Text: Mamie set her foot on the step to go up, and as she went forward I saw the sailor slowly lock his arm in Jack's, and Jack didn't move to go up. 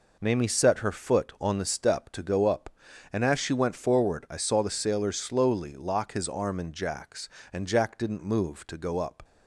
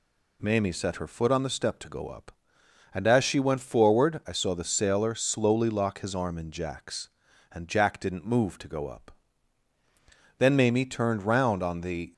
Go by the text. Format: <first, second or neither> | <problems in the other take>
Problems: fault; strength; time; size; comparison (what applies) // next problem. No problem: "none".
first | goes on to say "Then Mamie turned round on the"; strong; from 10.3 s on; 1.7 s long